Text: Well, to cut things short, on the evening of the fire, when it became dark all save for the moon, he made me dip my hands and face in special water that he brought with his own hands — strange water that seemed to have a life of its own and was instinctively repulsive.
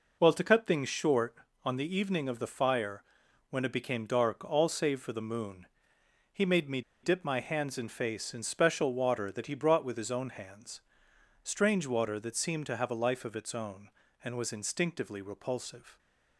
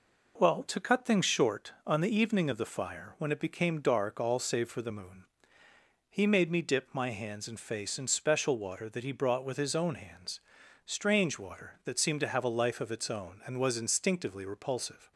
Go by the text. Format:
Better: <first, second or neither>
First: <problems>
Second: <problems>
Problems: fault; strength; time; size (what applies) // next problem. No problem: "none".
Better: second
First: pauses between "me" and "dip"; slight; at 6.8 s; 0.22 s long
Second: none